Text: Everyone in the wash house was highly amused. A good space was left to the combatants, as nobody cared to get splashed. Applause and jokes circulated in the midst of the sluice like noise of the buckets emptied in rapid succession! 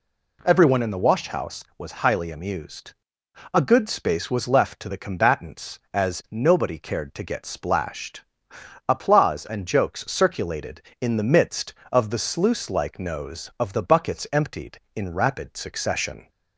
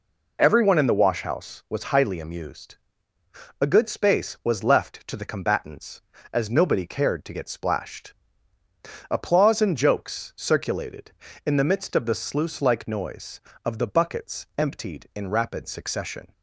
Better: second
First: says "nose" for "noise"; at 12.9 s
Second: none

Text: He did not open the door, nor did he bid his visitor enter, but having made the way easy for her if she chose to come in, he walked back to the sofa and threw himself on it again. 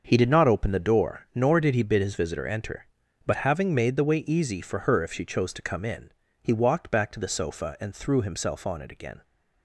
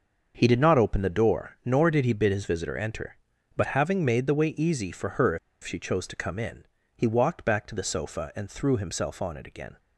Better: first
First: starts louder than the rest; until 1.0 s; 6.5 dB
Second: starts louder than the rest; until 1.3 s; 6.5 dB // pauses between "if" and "she"; slight; at 5.3 s; 0.25 s long

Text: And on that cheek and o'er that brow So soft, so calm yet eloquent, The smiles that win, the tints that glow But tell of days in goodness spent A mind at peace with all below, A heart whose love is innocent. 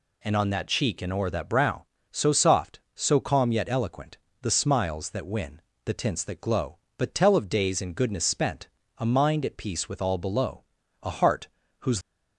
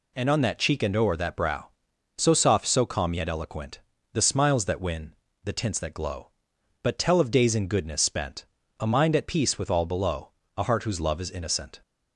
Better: second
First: pauses between "spent" and "A"; slight; at 8.6 s; 0.30 s long // pauses between "heart" and "whose"; slight; at 11.4 s; 0.32 s long // stops before "love is innocent"; at 12.0 s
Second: pauses between "spent" and "A"; slight; at 8.4 s; 0.34 s long

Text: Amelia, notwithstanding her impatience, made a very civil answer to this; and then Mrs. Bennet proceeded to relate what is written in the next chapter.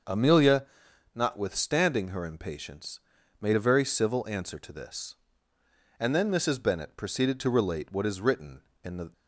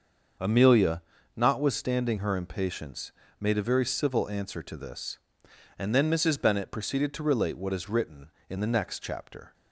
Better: second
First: starts louder than the rest; until 1.5 s; 6.5 dB // stops before "next chapter"; at 9.1 s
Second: starts louder than the rest; until 1.7 s; 6.5 dB

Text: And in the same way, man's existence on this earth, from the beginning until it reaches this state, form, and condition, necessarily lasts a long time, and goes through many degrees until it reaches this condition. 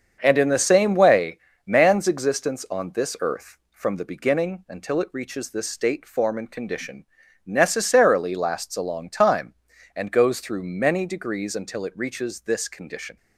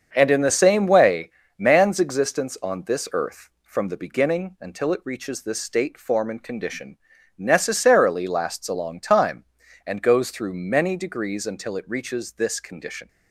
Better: neither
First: starts louder than the rest; until 1.2 s; 7 dB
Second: starts louder than the rest; until 1.1 s; 6.5 dB

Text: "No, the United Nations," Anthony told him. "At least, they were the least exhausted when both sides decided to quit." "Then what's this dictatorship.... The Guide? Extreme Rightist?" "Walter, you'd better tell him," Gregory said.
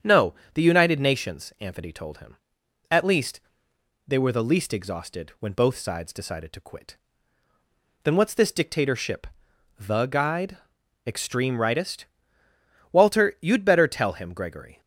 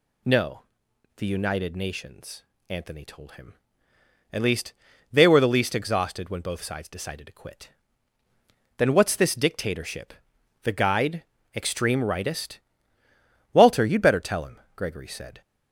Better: second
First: starts louder than the rest; strong; until 1.2 s; 8 dB // stops before "said"; at 14.8 s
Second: none

